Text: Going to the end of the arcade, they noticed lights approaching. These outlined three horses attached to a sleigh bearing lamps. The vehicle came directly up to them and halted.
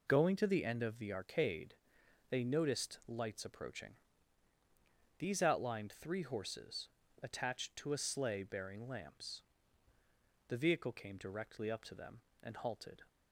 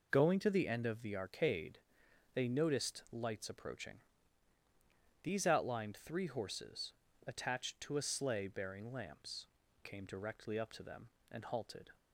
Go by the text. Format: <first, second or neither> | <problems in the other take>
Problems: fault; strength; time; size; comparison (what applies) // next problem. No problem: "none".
first | pauses between "horses" and "attached"; slight; at 6.9 s; 0.34 s long; slight in the first // skips "The vehicle"; at 9.6 s